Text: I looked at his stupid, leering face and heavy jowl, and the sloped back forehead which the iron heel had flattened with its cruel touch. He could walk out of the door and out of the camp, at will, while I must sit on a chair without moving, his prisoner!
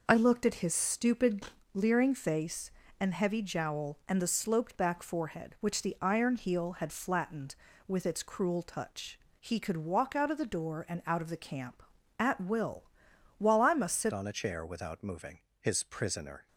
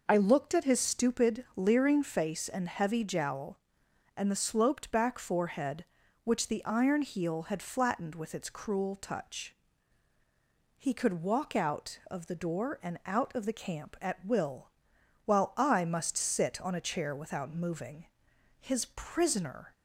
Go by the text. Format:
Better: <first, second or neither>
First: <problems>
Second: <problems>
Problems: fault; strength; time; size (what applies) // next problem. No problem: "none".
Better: second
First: changes voice at "on"; from 14.1 s on; 2.3 s long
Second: none